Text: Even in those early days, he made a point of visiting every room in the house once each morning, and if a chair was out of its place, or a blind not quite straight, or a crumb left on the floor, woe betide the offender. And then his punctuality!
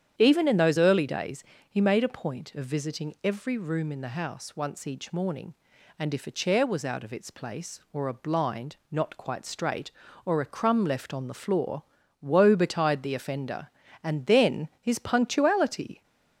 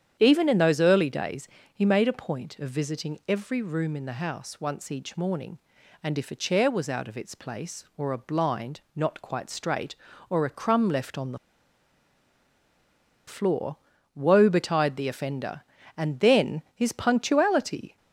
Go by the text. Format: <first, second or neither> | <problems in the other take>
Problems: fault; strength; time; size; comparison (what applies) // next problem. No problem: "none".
first | starts louder than the rest; strong; until 1.2 s; 9 dB; strong in the first // pauses between "the" and "floor"; strong; at 11.3 s; 1.9 s long